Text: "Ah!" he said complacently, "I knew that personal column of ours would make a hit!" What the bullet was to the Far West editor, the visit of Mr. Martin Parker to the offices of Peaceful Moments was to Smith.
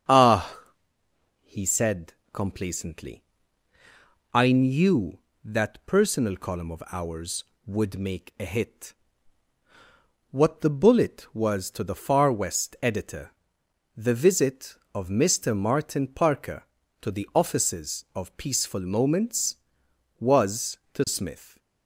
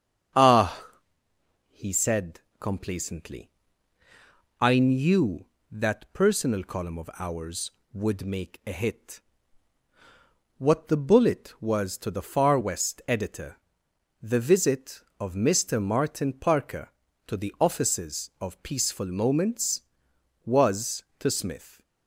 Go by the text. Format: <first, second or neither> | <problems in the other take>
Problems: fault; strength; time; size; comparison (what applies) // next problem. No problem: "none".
neither | starts louder than the rest; strong; the same in both // pauses between "said" and "complacently"; slight; the same in both